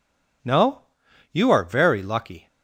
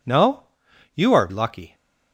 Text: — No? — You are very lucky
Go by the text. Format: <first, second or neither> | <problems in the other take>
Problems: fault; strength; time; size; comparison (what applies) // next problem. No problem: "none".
first | skips "very"; at 1.2 s